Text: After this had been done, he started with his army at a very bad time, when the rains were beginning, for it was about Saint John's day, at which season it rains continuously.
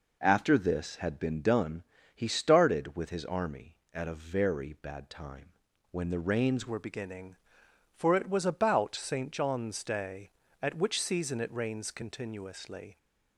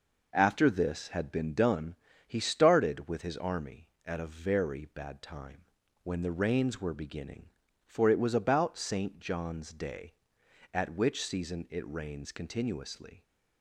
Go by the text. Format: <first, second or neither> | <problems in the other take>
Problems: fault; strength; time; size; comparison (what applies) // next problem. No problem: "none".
second | changes voice at "were"; from 6.6 s on; 6.3 s long